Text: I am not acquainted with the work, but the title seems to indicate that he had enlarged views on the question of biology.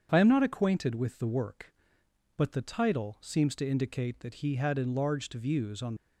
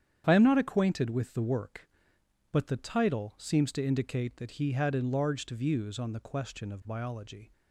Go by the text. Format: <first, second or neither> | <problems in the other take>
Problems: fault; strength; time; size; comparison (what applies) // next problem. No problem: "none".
second | starts louder than the rest; strong; until 1.1 s; 7.5 dB; strong in the second // stops before "the question of biology"; at 5.9 s